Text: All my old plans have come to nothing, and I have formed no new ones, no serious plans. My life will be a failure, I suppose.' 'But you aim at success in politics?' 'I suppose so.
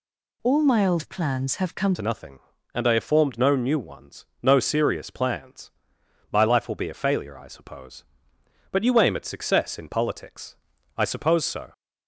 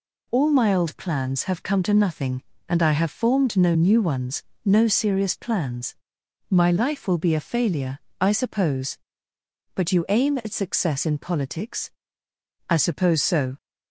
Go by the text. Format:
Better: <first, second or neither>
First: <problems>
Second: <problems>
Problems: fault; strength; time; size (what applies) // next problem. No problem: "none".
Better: second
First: changes voice at "to"; from 1.9 s on; 9.8 s long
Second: none